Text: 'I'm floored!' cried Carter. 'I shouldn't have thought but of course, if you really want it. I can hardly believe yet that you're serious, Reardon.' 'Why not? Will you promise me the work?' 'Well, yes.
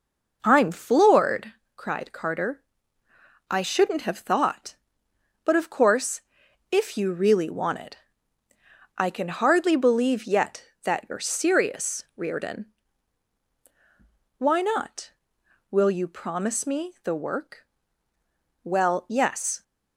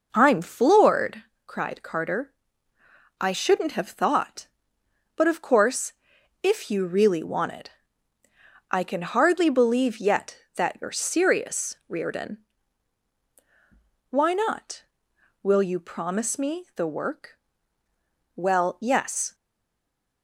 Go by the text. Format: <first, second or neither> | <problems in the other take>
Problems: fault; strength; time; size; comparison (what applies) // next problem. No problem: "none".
first | stays silent after the last word; slight; from 19.3 s on; 0.9 s long